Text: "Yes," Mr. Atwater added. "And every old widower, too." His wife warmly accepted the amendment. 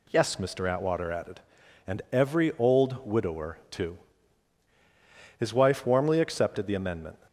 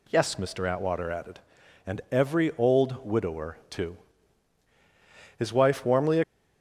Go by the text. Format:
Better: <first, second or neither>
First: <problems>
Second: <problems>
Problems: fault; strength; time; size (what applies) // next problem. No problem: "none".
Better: first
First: none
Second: stops before "accepted the amendment"; at 6.2 s